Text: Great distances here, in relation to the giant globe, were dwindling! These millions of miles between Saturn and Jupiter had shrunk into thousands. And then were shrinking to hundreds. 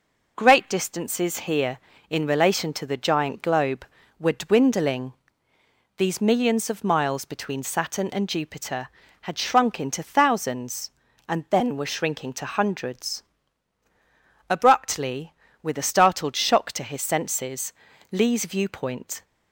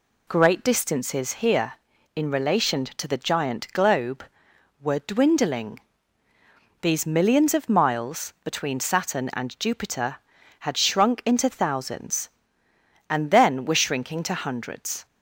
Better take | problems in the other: second | goes on to say "Abruptly with a startled shock to his senses Lee's viewpoint"; strong; from 14.4 s on; 4.7 s long

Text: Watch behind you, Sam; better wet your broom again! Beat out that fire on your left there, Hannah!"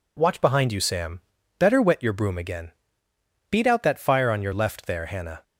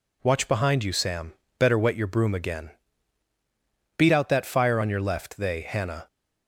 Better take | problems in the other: first | says "they" for "there"; at 5.3 s

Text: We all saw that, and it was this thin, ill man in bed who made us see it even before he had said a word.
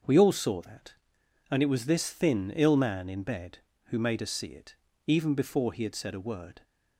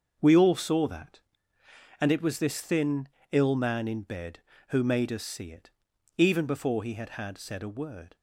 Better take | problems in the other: first | starts louder than the rest; until 1.2 s; 6.5 dB; also in the first // pauses between "it" and "even"; noticeable; at 5.6 s; 0.50 s long; slight in the first // says "had" twice; at 7.0 s

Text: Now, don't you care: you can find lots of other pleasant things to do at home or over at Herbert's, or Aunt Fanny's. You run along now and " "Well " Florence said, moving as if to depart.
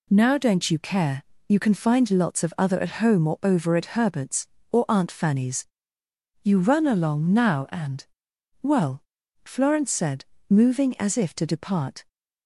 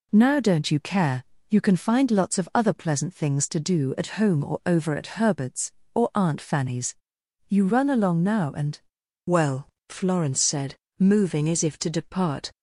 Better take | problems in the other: second | skips "pleasant things to do"; at 2.8 s

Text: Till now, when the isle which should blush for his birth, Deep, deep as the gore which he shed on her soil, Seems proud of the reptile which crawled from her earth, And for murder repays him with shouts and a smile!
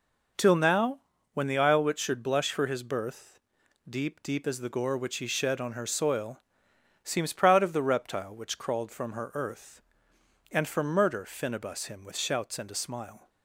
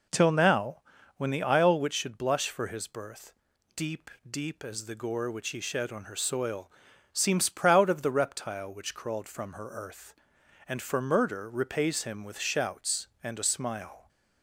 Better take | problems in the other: second | says "finibus" for "repays"; at 11.2 s

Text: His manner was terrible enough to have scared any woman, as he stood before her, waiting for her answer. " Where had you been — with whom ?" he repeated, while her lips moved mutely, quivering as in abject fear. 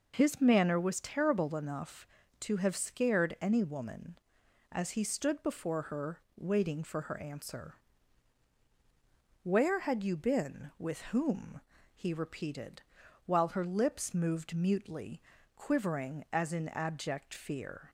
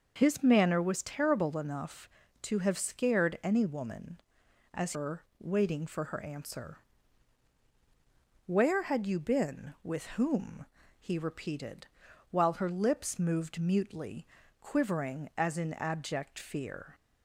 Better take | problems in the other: first | skips "he stood before"; at 4.9 s

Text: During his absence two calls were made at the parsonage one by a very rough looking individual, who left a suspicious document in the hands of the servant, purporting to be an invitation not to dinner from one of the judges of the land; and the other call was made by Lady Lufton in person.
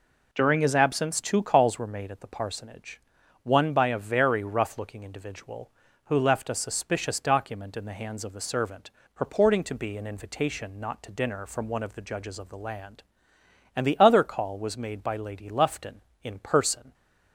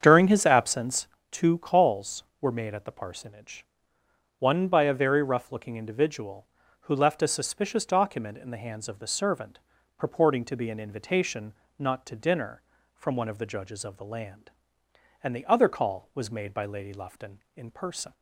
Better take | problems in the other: first | starts louder than the rest; strong; until 1.2 s; 8 dB // pauses between "absence" and "two"; slight; at 1.0 s; 0.24 s long // pauses between "parsonage" and "one"; noticeable; at 3.6 s; 0.76 s long; also in the first // pauses between "invitation" and "not"; slight; at 11.5 s; 0.24 s long

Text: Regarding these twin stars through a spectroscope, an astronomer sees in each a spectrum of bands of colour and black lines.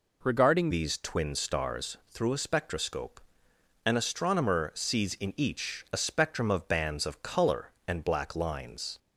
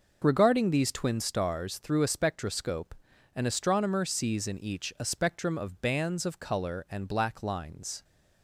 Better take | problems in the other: second | changes voice at "these"; from 0.7 s on; 8.2 s long

